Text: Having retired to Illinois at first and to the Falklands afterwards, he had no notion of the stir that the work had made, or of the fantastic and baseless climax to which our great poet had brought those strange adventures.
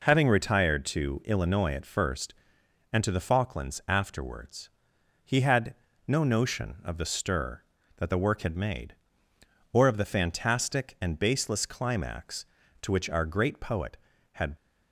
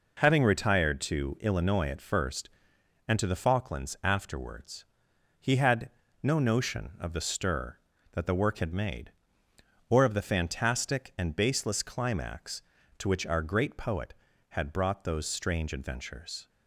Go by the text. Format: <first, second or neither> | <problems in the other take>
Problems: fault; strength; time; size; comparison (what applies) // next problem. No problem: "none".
second | pauses between "had" and "no"; slight; at 5.7 s; 0.34 s long; slight in the second // stops before "brought those strange adventures"; at 14.5 s